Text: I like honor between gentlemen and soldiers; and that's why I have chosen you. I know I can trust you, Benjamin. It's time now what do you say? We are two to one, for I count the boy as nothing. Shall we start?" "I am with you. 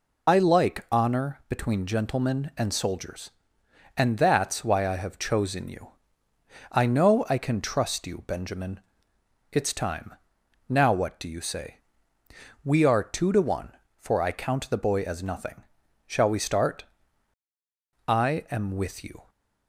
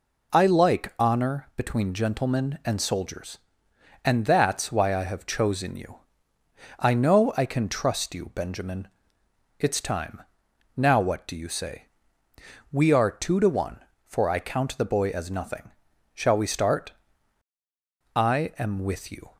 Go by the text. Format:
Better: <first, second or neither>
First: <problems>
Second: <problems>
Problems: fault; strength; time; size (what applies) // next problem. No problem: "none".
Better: second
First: loses the start of "I"; at 0.2 s; 30 ms // pauses between "time" and "now"; noticeable; at 10.1 s; 0.52 s long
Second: pauses between "time" and "now"; noticeable; at 10.2 s; 0.52 s long